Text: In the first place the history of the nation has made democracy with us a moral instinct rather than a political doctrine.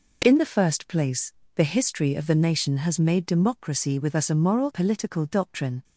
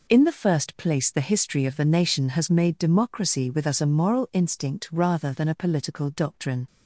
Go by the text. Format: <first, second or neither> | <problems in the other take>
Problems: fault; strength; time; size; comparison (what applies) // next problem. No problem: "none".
second | pauses between "place" and "the"; slight; at 1.3 s; 0.24 s long // skips "instinct rather than a"; at 4.7 s